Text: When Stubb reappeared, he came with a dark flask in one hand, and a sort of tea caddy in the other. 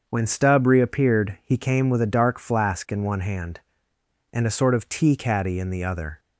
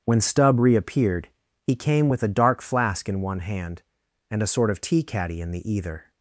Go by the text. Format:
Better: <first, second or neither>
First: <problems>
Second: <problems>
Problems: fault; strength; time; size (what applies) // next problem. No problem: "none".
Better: first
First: starts louder than the rest; until 1.0 s; 6.5 dB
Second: starts louder than the rest; strong; until 1.0 s; 7.5 dB // says "either" for "other"; at 5.7 s